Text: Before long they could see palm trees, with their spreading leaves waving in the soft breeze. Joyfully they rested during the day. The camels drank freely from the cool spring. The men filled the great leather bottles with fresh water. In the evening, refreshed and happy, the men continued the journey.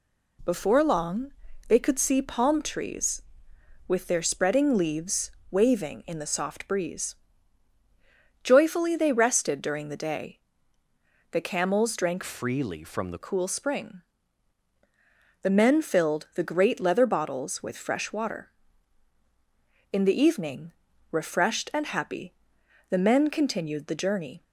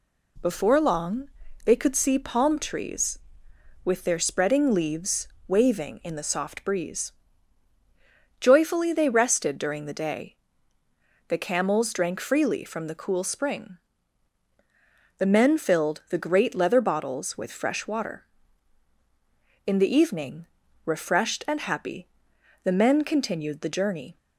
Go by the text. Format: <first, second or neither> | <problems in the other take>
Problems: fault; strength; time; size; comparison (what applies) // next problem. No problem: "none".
second | pauses between "long" and "they"; slight; at 1.3 s; 0.36 s long; slight in the second // pauses between "leaves" and "waving"; slight; at 5.2 s; 0.20 s long; slight in the second // changes voice from "freely" to "the"; from 12.2 to 13.1 s; 0.9 s long